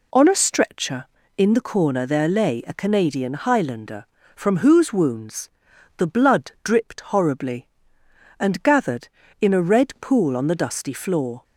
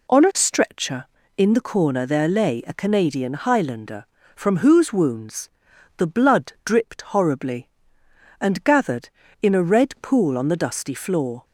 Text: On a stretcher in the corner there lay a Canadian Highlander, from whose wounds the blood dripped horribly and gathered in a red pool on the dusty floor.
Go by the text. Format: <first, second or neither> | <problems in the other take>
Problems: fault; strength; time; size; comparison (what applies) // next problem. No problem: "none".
neither | pauses between "wounds" and "the"; noticeable; the same in both